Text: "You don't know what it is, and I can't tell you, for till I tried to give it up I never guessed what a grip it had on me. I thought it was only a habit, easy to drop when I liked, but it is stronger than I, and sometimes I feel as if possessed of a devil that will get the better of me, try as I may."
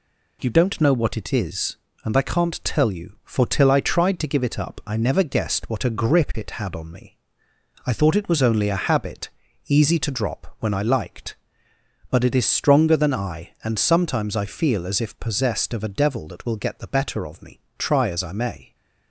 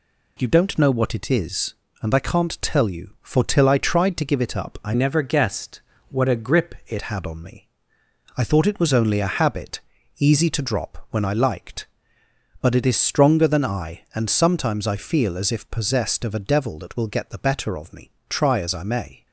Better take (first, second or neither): first